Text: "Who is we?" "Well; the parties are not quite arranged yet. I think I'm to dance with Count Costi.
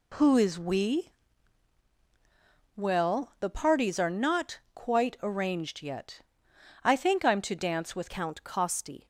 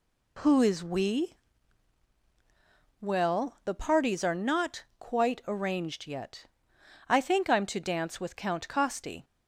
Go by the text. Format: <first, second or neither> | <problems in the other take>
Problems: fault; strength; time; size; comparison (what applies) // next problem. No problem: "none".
second | pauses between "not" and "quite"; slight; at 4.5 s; 0.16 s long; slight in the second // changes voice at "Count"; from 8.0 s on; 1.0 s long